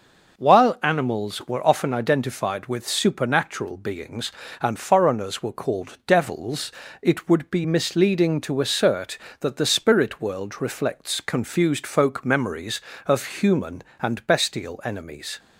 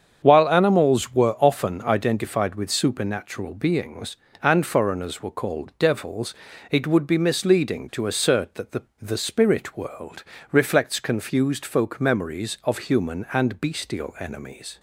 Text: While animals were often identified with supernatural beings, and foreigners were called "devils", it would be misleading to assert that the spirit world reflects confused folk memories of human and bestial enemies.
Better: first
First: none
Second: starts louder than the rest; strong; until 1.2 s; 7.5 dB // says "the" twice; at 8.9 s // pauses between "world" and "reflects"; slight; at 10.2 s; 0.26 s long

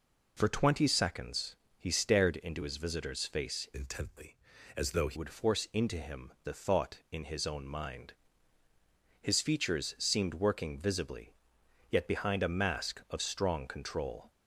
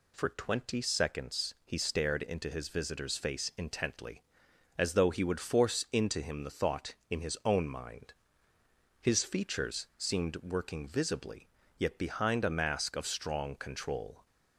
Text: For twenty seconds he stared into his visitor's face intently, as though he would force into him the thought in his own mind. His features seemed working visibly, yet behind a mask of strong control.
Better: second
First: pauses between "seconds" and "he"; slight; at 1.5 s; 0.24 s long // changes voice from "intently" to "he"; from 3.7 to 5.1 s; 1.4 s long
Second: none

